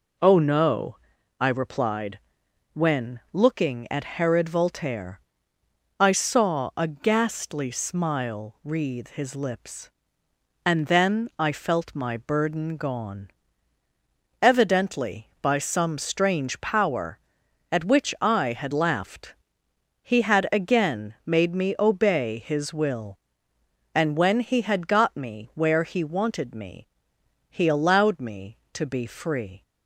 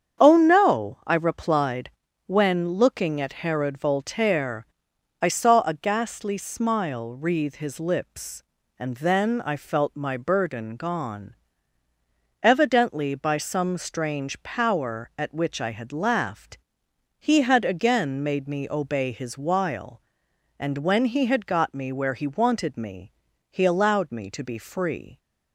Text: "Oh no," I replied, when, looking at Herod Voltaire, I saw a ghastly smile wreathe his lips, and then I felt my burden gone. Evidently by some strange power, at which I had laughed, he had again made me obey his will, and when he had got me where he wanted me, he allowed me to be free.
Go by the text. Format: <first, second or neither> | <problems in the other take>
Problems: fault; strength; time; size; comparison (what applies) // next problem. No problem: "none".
first | starts louder than the rest; strong; until 1.2 s; 8 dB // says "while" for "will"; at 19.3 s